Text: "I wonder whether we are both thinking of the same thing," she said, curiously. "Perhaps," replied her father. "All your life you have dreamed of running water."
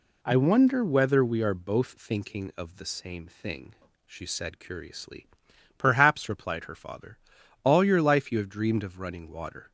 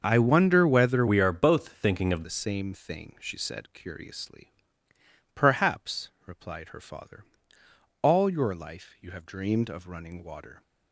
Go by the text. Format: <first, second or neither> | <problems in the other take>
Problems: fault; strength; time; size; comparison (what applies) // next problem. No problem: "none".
first | starts louder than the rest; until 1.0 s; 6.5 dB // changes voice from "we" to "of"; from 1.0 to 2.2 s; 1.2 s long